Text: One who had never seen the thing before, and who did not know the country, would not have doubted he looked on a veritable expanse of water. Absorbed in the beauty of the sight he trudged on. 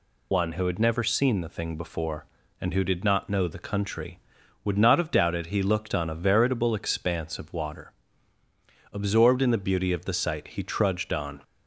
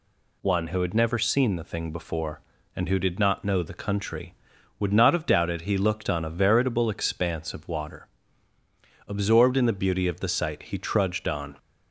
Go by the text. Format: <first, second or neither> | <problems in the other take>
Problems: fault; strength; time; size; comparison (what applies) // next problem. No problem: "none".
second | loses the start of "One"; at 0.3 s; 55 ms